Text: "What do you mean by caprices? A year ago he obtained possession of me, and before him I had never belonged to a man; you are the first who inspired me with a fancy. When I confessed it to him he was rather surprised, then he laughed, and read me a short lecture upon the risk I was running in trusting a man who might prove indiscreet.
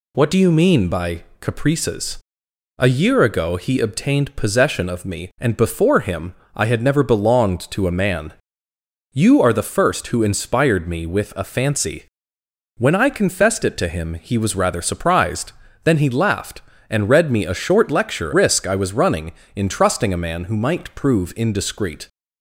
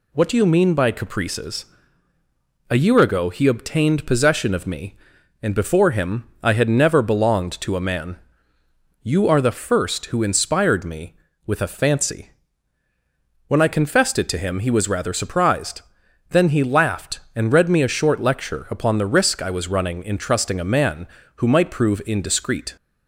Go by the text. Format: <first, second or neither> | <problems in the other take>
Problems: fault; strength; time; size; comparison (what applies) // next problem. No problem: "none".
second | pauses between "by" and "caprices"; slight; at 1.2 s; 0.18 s long // pauses between "him" and "I"; slight; at 6.3 s; 0.22 s long; slight in the second // skips "upon the"; at 18.3 s